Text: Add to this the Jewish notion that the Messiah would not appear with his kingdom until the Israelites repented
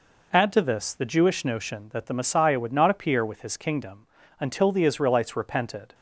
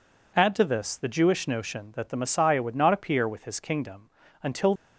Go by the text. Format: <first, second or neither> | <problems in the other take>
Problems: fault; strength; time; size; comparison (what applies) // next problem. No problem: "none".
first | pauses between "kingdom" and "until"; slight; at 4.0 s; 0.32 s long; slight in the first // stops before "the Israelites repented"; at 4.7 s